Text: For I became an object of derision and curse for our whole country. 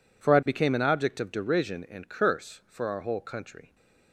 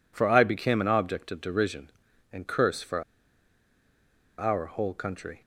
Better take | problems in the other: first | pauses between "for" and "our"; strong; at 3.0 s; 1.3 s long

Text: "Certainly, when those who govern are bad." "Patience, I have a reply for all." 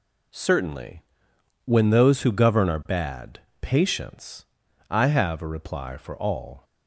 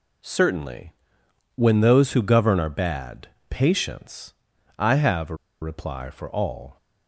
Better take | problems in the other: first | pauses between "a" and "reply"; slight; at 5.3 s; 0.25 s long

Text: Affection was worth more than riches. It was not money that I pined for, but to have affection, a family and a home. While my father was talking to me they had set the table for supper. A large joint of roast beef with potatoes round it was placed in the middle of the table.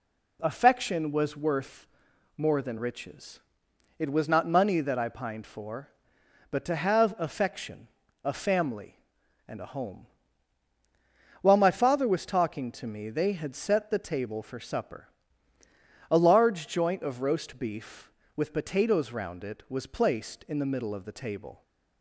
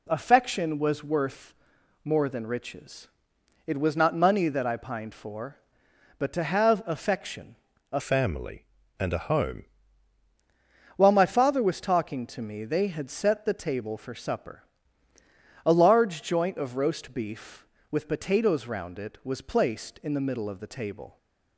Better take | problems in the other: first | pauses between "worth" and "more"; noticeable; at 1.5 s; 0.50 s long; noticeable in the first // changes voice from "family" to "home"; from 7.9 to 9.6 s; 1.7 s long

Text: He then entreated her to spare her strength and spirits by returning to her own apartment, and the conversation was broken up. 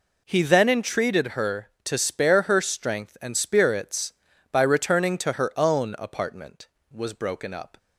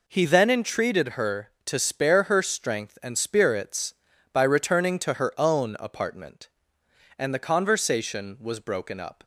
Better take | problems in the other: second | skips "and the conversation"; at 6.7 s

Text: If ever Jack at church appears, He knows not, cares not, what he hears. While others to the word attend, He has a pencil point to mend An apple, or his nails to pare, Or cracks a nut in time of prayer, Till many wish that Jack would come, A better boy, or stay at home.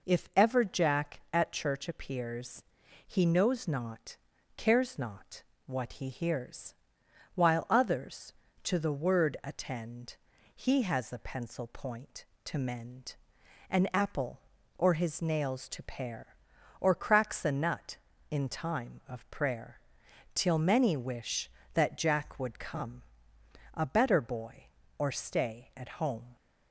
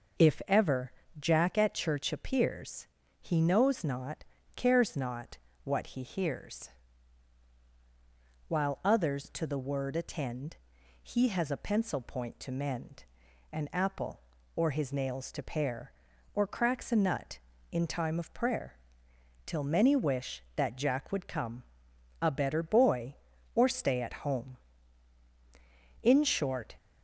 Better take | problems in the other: first | pauses between "ever" and "Jack"; slight; at 0.9 s; 0.26 s long // pauses between "mend" and "An"; noticeable; at 13.0 s; 0.48 s long; noticeable in the first // goes on to say "In short"; noticeable; from 26.0 s on; 0.74 s long

